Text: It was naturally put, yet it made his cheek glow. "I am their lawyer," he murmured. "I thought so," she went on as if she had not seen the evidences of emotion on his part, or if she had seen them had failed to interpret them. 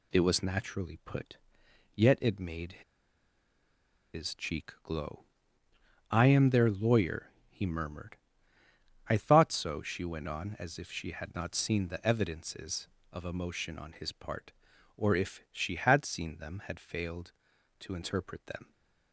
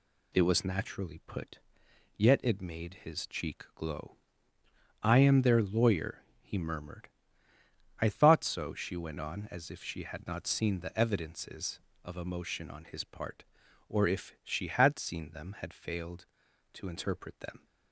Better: second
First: pauses between "made" and "his"; strong; at 2.7 s; 1.3 s long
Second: none

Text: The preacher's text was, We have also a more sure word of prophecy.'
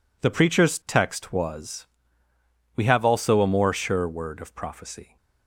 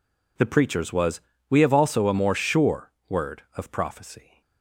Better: first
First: none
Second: skips "text"; at 0.9 s // pauses between "sure" and "word"; slight; at 2.9 s; 0.16 s long

